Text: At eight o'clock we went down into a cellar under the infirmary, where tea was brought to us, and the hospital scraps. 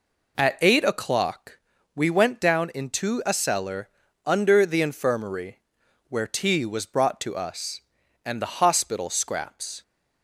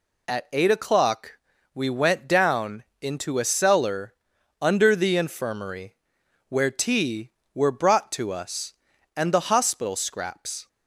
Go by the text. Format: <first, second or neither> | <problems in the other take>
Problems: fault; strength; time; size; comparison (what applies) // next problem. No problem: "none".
first | pauses between "o'clock" and "we"; at 1.3 s; 0.40 s long; slight in the first // pauses between "down" and "into"; slight; at 2.8 s; 0.18 s long // pauses between "cellar" and "under"; noticeable; at 4.1 s; 0.46 s long; also in the first // says "were" for "was"; at 7.5 s